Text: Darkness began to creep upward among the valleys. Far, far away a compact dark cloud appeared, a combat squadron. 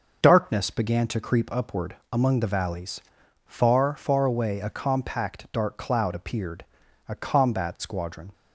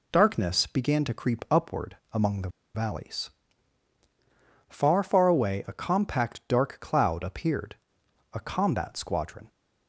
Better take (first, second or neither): first